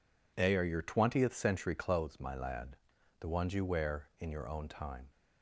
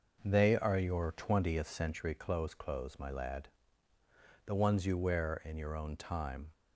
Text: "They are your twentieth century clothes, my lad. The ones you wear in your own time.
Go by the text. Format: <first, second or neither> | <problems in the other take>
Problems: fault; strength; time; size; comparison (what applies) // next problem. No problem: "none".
first | says "clothes" twice; at 2.5 s